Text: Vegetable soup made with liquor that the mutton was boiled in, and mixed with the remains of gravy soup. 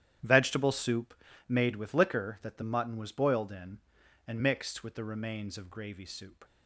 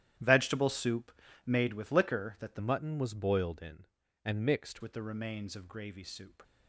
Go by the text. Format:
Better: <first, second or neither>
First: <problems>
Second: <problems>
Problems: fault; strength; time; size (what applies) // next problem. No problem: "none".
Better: first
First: starts louder than the rest; strong; until 1.5 s; 10.5 dB // pauses between "soup" and "made"; slight; at 1.1 s; 0.34 s long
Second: starts louder than the rest; strong; until 1.5 s; 11.5 dB // pauses between "soup" and "made"; slight; at 1.1 s; 0.34 s long // changes voice from "mutton" to "mixed"; from 2.5 to 4.8 s; 2.3 s long